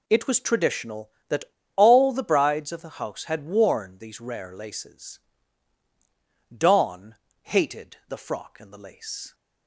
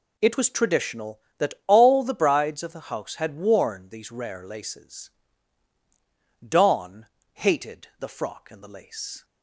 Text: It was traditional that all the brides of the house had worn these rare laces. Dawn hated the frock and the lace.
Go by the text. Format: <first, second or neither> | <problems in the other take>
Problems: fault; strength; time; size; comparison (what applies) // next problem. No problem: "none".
second | pauses between "that" and "all"; slight; at 1.4 s; 0.30 s long // pauses between "Dawn" and "hated"; slight; at 7.1 s; 0.26 s long; slight in the second